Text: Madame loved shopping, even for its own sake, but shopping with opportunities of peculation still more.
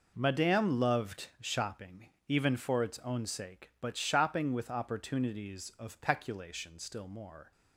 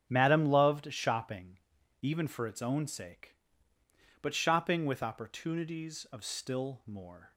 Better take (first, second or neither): first